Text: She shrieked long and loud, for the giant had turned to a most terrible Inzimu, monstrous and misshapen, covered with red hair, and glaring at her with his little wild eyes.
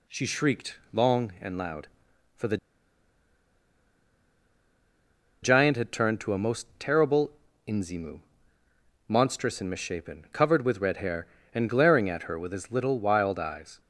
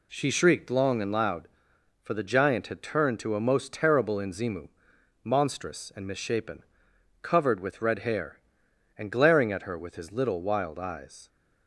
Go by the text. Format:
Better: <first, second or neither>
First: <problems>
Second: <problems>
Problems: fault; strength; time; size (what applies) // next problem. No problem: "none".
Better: second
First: pauses between "the" and "giant"; strong; at 2.5 s; 2.8 s long // pauses between "terrible" and "Inzimu"; slight; at 7.3 s; 0.34 s long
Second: none